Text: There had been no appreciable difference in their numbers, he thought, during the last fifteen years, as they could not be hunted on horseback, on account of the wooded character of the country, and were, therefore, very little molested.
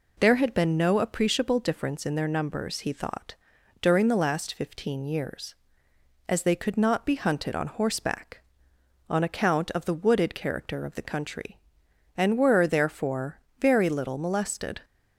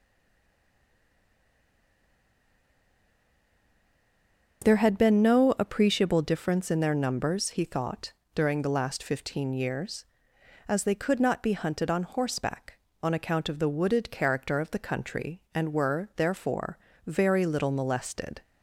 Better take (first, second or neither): first